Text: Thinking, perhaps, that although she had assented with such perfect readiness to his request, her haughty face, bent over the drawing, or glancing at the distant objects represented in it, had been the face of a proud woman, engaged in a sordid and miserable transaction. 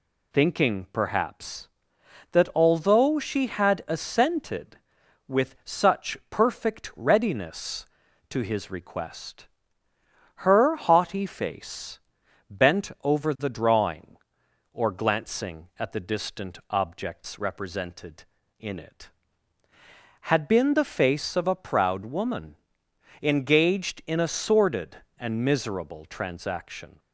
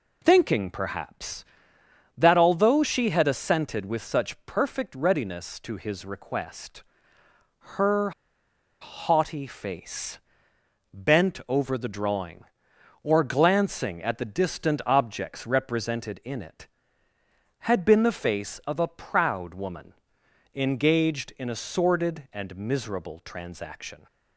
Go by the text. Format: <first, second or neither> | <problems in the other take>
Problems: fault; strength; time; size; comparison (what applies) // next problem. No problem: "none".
first | pauses between "her" and "haughty"; noticeable; at 8.1 s; 0.70 s long